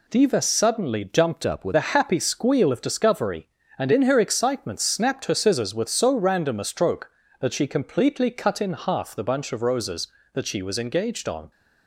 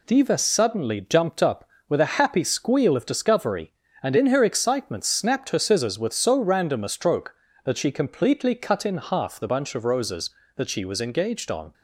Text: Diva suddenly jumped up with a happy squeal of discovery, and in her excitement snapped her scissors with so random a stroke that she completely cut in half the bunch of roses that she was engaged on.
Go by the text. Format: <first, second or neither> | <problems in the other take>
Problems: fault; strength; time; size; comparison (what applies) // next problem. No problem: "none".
second | changes voice from "up" to "with"; from 1.4 to 1.7 s; 0.3 s long